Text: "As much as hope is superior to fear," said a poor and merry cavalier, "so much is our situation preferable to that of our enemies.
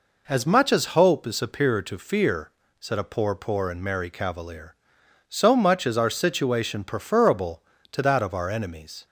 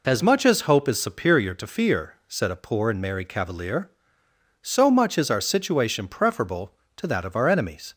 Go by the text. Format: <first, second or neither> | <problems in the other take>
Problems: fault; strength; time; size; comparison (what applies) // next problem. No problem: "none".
second | says "poor" twice; at 3.3 s